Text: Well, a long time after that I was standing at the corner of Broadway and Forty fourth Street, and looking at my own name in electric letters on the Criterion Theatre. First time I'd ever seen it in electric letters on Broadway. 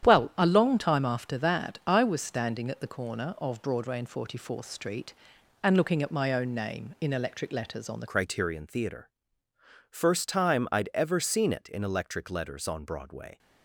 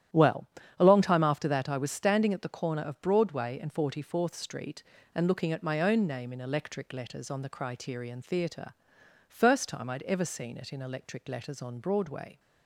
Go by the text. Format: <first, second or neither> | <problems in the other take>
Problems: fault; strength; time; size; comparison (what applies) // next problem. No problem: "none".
second | starts louder than the rest; strong; until 1.1 s; 10 dB; strong in the second // changes voice at "Criterion"; from 8.0 s on; 5.3 s long